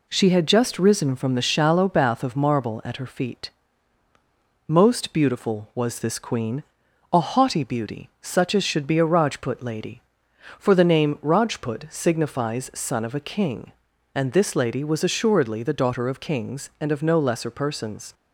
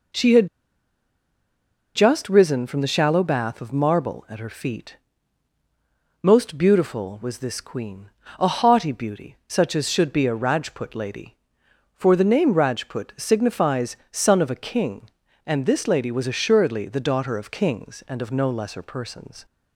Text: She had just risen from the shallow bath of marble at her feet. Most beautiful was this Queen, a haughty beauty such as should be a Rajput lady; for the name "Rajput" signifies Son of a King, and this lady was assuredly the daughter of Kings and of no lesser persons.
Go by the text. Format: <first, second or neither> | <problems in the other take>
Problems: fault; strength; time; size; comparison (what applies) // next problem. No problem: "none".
first | pauses between "had" and "just"; strong; at 0.4 s; 1.4 s long // pauses between "signifies" and "Son"; slight; at 13.9 s; 0.16 s long